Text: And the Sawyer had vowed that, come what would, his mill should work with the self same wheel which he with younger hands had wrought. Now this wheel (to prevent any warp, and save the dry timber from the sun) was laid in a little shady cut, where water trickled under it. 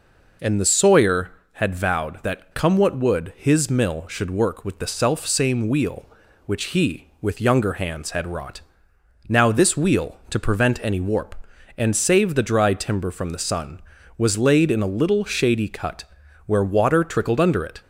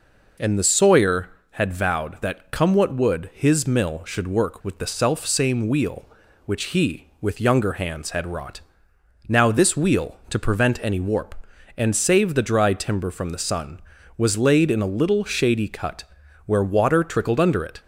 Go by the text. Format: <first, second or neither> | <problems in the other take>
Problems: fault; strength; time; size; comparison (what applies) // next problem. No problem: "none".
neither | none